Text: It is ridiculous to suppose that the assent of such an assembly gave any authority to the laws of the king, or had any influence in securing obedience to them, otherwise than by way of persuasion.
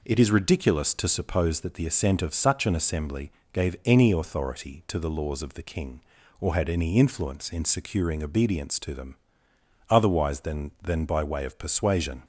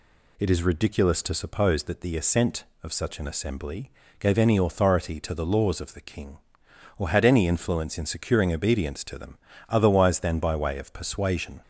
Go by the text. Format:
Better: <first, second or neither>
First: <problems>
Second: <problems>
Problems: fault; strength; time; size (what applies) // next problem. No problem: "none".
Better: second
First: pauses between "assembly" and "gave"; slight; at 3.3 s; 0.22 s long // says "than" twice; at 10.8 s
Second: pauses between "assembly" and "gave"; slight; at 3.8 s; 0.30 s long